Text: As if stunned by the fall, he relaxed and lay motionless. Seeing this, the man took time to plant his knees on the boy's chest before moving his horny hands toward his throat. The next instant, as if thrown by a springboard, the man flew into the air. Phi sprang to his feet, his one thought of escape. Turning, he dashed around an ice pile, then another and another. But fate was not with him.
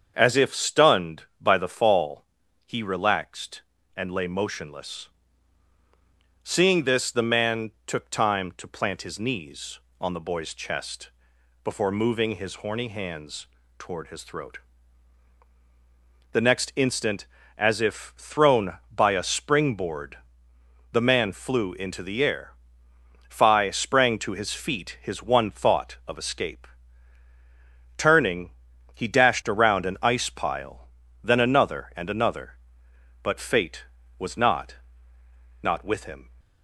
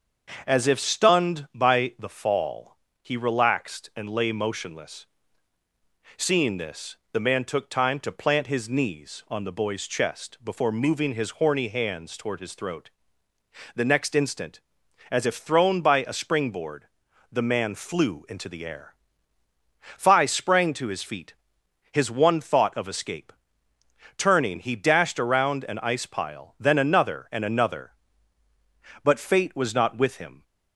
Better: second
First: starts louder than the rest; strong; until 1.1 s; 7 dB // pauses between "chest" and "before"; noticeable; at 11.0 s; 0.56 s long // pauses between "hands" and "toward"; slight; at 13.4 s; 0.30 s long // says "not" twice; at 35.6 s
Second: starts louder than the rest; until 1.4 s; 6.5 dB

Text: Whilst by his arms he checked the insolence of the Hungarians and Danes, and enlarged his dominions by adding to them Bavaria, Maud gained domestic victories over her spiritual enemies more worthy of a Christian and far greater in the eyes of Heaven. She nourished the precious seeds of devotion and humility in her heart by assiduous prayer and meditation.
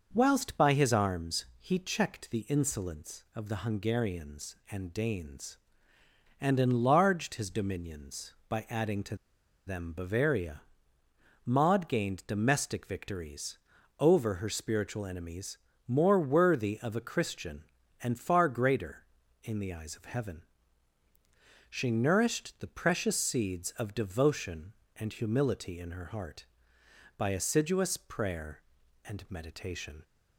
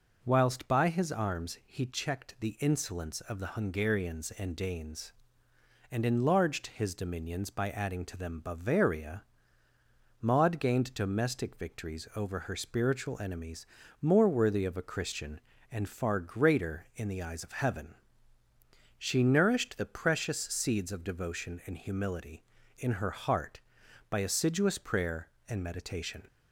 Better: second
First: starts louder than the rest; until 1.1 s; 6 dB // pauses between "to" and "them"; noticeable; at 9.1 s; 0.50 s long // pauses between "victories" and "over"; at 13.5 s; 0.42 s long // pauses between "enemies" and "more"; slight; at 15.5 s; 0.30 s long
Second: pauses between "enemies" and "more"; slight; at 13.6 s; 0.34 s long

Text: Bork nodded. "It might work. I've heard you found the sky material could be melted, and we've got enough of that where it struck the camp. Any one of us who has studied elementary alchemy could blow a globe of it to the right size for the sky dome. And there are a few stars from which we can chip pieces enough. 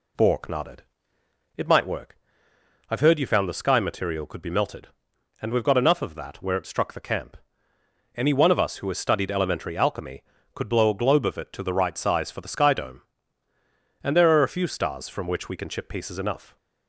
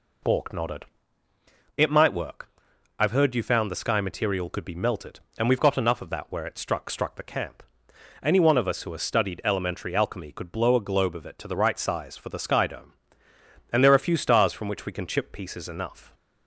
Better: first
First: none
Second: says "struck" twice; at 6.8 s

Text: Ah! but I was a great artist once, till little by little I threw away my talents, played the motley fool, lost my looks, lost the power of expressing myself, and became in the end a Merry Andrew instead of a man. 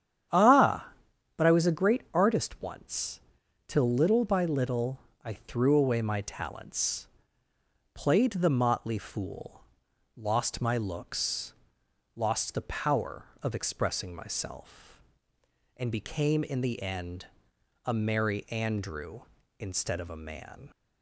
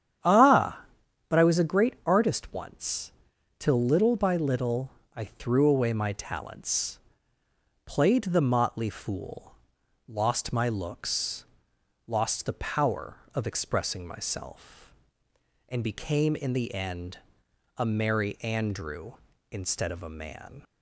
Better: neither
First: starts louder than the rest; strong; until 1.7 s; 9.5 dB // pauses between "little" and "I"; slight; at 4.9 s; 0.26 s long // pauses between "end" and "a"; noticeable; at 17.2 s; 0.60 s long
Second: starts louder than the rest; strong; until 1.6 s; 9.5 dB // pauses between "little" and "I"; slight; at 4.8 s; 0.26 s long // pauses between "end" and "a"; noticeable; at 17.1 s; 0.60 s long

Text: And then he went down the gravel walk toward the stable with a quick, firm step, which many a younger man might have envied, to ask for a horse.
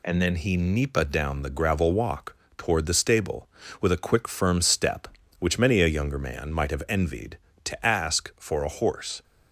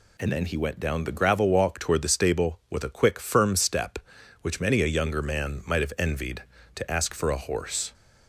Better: second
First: says "nipa" for "went"; at 0.5 s // pauses between "walk" and "toward"; slight; at 2.3 s; 0.22 s long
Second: none

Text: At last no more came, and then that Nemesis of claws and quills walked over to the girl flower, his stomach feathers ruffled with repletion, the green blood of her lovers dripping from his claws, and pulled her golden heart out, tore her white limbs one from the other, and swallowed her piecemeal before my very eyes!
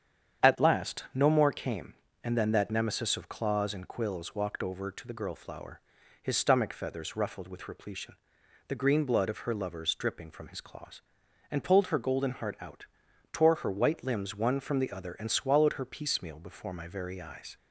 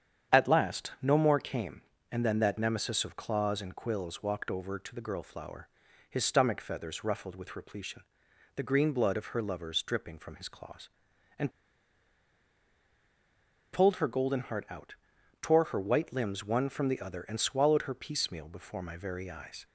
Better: first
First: starts louder than the rest; strong; until 1.5 s; 8.5 dB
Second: starts louder than the rest; strong; until 1.4 s; 8.5 dB // pauses between "and" and "pulled"; strong; at 11.5 s; 2.2 s long

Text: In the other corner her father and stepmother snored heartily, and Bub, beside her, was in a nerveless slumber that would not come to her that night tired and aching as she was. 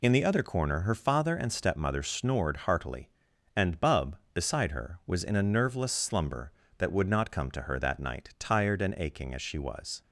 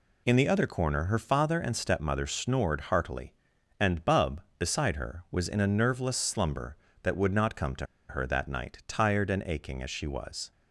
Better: first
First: none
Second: pauses between "to" and "her"; slight; at 7.8 s; 0.22 s long

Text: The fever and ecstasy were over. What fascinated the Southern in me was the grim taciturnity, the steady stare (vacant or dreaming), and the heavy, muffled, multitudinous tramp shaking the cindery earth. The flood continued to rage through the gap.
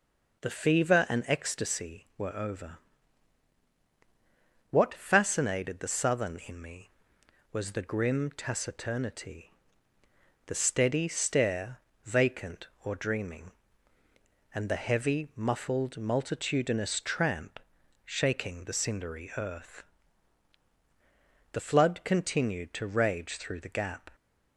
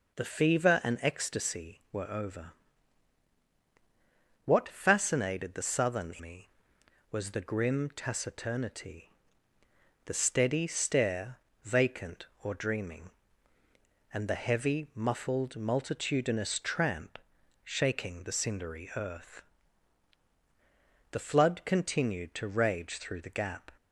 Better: first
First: pauses between "tramp" and "shaking"; noticeable; at 17.5 s; 0.46 s long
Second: skips "in"; at 6.1 s // pauses between "tramp" and "shaking"; noticeable; at 17.1 s; 0.46 s long

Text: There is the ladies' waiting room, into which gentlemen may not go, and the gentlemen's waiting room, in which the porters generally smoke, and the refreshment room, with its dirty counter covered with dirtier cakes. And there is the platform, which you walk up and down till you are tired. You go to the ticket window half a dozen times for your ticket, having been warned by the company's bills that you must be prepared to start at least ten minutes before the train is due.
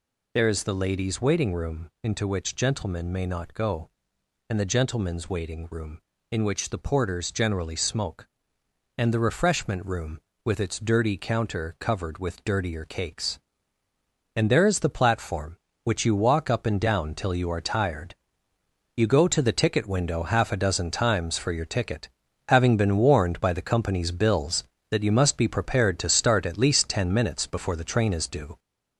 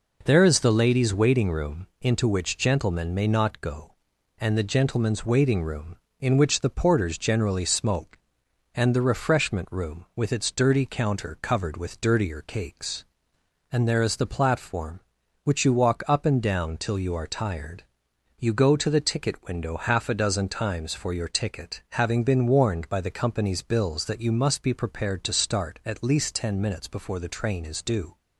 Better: second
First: gets louder; noticeable; throughout; 4.5 dB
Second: none

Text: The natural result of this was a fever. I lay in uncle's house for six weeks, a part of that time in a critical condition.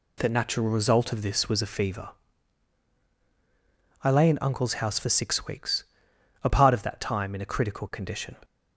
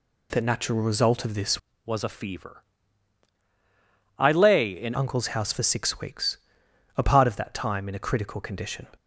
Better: first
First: none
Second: changes voice from "was" to "in"; from 1.8 to 4.9 s; 3.1 s long

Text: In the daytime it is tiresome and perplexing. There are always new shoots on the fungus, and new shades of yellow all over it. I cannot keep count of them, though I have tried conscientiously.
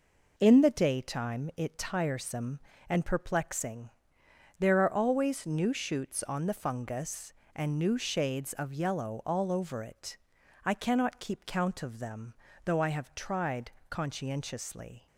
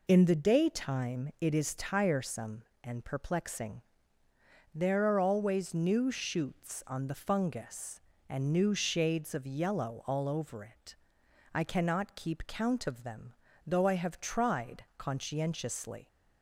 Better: second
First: skips "is"; at 1.7 s // pauses between "tried" and "conscientiously"; slight; at 13.7 s; 0.18 s long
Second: none

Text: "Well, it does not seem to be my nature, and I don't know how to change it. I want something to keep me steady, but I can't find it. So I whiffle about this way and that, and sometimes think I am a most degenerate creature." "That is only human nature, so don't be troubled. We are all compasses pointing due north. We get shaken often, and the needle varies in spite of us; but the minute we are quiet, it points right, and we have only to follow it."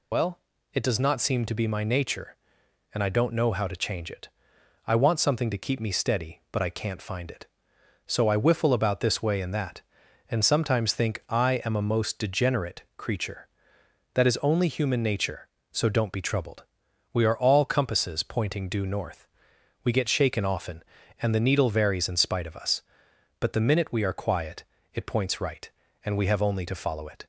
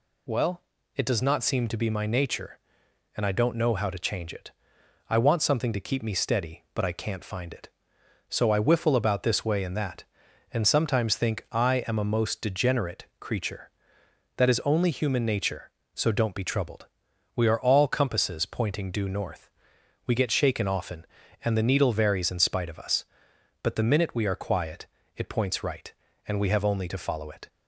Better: second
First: loses the start of "Well"; at 0.1 s; 75 ms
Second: none

